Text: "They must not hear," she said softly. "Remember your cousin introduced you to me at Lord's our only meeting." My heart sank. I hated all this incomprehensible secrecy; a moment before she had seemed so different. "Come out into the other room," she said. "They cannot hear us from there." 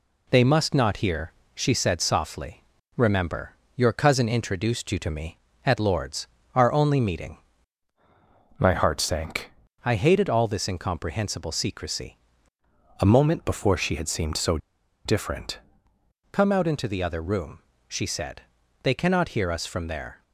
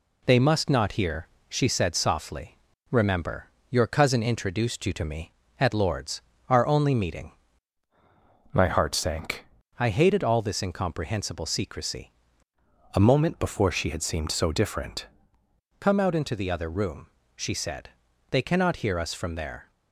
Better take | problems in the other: second | pauses between "Remember" and "your"; slight; at 3.5 s; 0.24 s long; slight in the second // pauses between "Lord's" and "our"; slight; at 6.2 s; 0.30 s long; slight in the second // pauses between "so" and "different"; noticeable; at 14.5 s; 0.47 s long

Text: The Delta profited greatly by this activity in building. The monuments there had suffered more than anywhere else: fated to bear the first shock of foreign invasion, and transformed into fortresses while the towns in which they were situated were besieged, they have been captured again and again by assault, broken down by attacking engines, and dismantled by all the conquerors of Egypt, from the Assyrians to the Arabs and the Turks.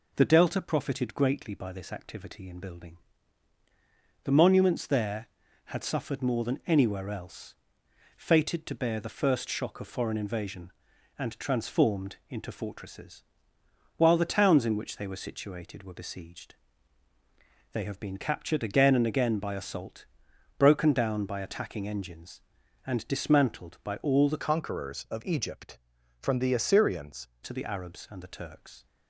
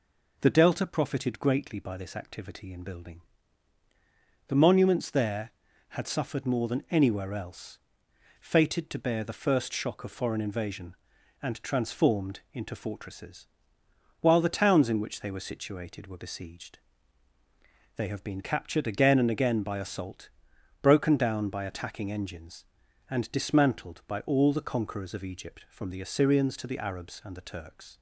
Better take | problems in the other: second | pauses between "fortresses" and "while"; noticeable; at 13.2 s; 0.74 s long; noticeable in the second // changes voice from "conquerors" to "Assyrians"; from 24.4 to 27.2 s; 2.8 s long

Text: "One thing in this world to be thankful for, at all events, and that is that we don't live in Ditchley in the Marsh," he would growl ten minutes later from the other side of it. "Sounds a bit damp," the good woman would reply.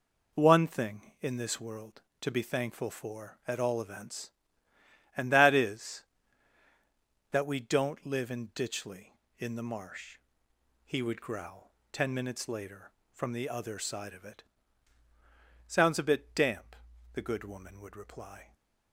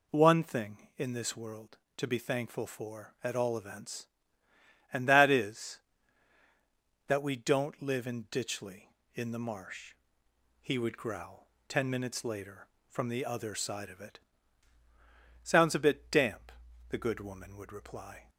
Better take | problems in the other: second | gets quieter; strong; throughout; 7 dB // pauses between "growl" and "ten"; slight; at 11.7 s; 0.16 s long; slight in the second

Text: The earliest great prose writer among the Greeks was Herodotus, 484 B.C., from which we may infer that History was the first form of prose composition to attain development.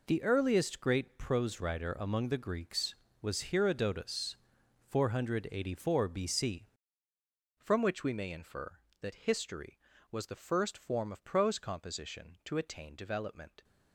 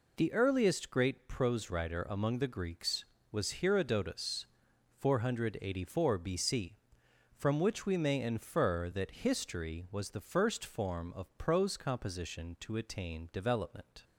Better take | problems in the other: second | changes voice at "from"; from 7.5 s on; 6.1 s long

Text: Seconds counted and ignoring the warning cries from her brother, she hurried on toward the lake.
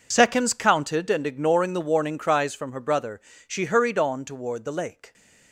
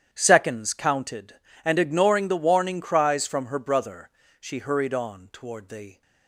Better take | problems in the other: first | starts louder than the rest; strong; until 1.1 s; 9.5 dB // stops before "lake"; at 6.0 s

